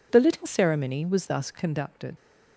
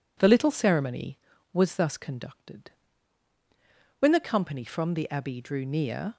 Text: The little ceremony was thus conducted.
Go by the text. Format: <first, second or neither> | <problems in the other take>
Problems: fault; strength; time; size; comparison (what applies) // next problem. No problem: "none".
first | goes on to say "When the company from the Abbey drew near"; strong; from 3.9 s on; 2.1 s long